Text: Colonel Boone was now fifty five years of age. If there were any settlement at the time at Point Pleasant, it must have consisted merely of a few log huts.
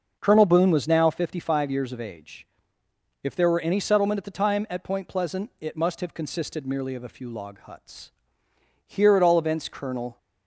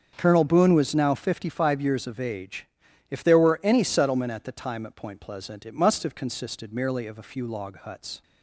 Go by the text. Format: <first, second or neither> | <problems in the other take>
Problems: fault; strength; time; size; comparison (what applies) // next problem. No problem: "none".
second | starts louder than the rest; until 1.2 s; 6.5 dB; also in the second // goes on to say "Here at all events Colonel"; from 8.8 s on; 1.3 s long